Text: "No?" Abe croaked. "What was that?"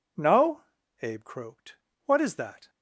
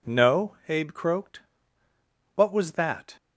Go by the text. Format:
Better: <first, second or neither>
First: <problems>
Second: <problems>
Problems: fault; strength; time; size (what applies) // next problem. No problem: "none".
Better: second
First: says "is" for "was"; at 2.2 s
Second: none